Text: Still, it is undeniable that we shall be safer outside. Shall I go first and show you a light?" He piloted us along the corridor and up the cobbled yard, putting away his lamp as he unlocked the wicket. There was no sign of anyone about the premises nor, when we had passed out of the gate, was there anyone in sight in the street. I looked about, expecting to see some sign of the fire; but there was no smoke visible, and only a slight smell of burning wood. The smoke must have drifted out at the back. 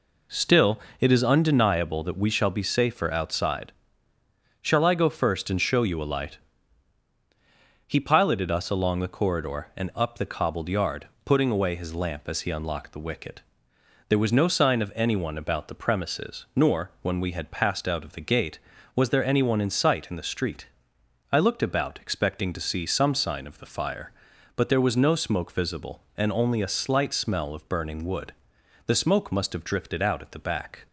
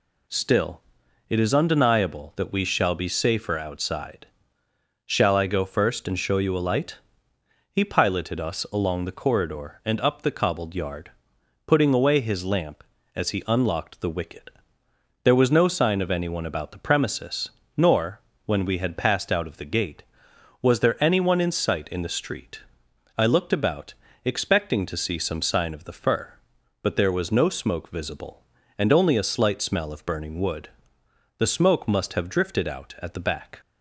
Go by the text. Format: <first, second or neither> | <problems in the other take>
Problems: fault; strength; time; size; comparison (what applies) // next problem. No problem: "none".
first | pauses between "premises" and "nor"; slight; at 17.4 s; 0.28 s long // says "fur" for "fire"; at 25.9 s